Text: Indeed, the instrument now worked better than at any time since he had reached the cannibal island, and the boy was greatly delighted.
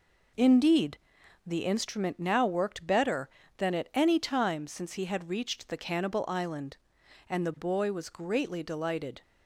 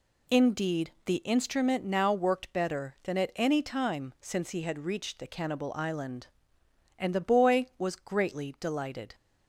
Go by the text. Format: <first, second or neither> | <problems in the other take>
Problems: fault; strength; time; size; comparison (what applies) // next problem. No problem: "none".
neither | none